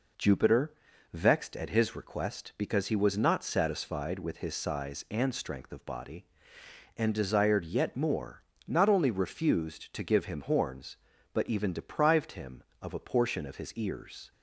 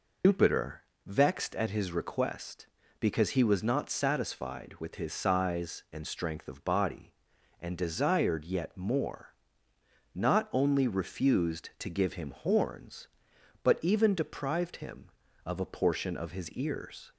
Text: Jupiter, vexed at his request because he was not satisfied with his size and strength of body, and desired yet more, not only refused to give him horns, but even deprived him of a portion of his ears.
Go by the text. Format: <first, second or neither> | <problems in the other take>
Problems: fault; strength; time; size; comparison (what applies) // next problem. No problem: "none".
first | loses the start of "Jupiter"; at 0.2 s; 115 ms